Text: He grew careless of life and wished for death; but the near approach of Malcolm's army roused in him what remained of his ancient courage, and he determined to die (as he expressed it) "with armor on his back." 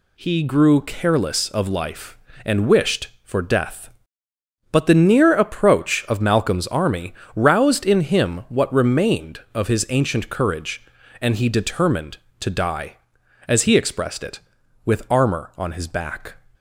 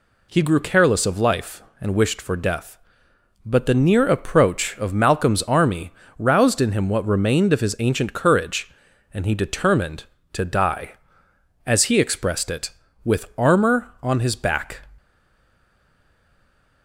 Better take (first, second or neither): first